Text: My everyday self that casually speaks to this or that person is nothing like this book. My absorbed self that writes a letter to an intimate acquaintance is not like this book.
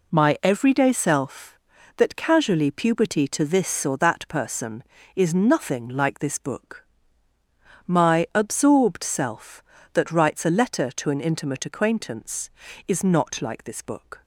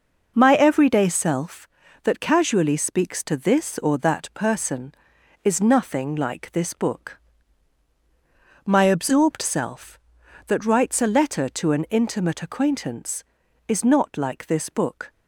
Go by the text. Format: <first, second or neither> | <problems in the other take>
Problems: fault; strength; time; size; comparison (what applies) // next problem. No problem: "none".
second | says "puberty" for "speaks"; at 2.7 s